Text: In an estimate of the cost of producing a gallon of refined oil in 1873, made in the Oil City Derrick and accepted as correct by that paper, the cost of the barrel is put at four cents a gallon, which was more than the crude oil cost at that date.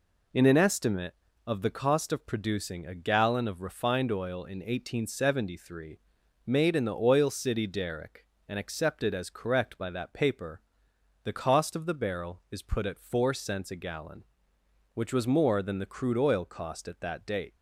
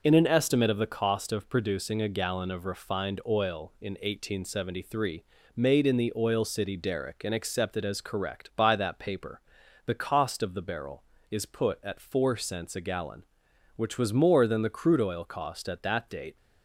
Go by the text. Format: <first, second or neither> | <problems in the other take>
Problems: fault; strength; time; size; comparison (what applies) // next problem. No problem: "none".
neither | none